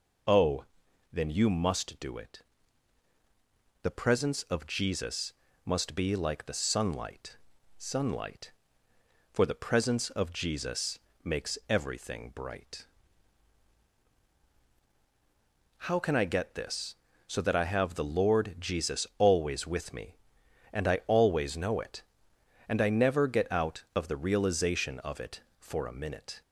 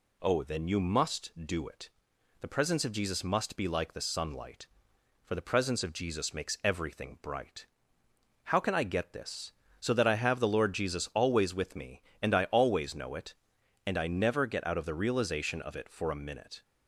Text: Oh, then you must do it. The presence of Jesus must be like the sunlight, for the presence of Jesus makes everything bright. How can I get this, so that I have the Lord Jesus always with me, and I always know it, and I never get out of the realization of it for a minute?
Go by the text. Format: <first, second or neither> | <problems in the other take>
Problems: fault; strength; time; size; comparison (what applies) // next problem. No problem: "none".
second | pauses between "Jesus" and "must"; slight; at 5.3 s; 0.32 s long // says "sunlight" twice; at 7.7 s // pauses between "Jesus" and "makes"; slight; at 10.9 s; 0.24 s long